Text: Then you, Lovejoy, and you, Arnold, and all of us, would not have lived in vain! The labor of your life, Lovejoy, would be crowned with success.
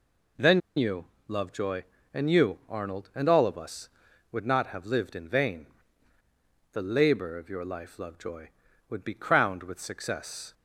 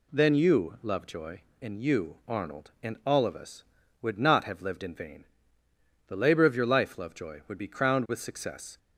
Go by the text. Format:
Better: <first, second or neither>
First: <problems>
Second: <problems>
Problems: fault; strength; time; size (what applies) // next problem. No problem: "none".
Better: second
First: pauses between "Then" and "you"; slight; at 0.5 s; 0.17 s long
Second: none